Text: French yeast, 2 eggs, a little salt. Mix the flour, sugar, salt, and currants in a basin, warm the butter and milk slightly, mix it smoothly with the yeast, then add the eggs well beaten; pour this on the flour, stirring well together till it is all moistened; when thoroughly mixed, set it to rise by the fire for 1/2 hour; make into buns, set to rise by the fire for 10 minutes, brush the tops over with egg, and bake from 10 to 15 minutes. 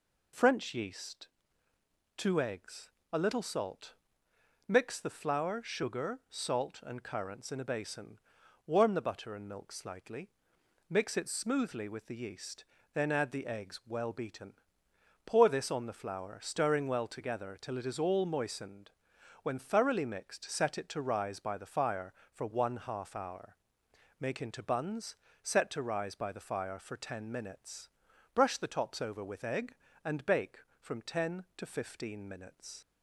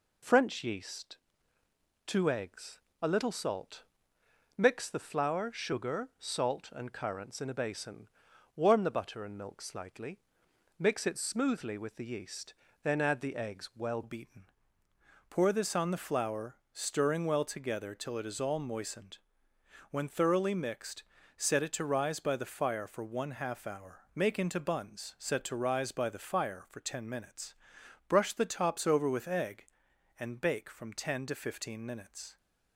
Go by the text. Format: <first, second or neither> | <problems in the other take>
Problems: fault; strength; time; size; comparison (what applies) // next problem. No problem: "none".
first | changes voice at "beaten"; from 14.0 s on; 18.3 s long